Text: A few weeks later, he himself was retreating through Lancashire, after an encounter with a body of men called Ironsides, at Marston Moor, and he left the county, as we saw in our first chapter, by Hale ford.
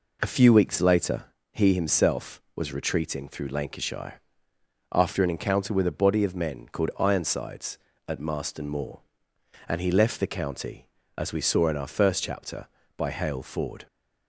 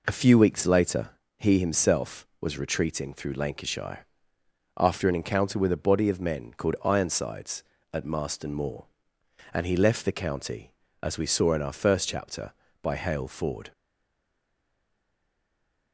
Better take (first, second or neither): first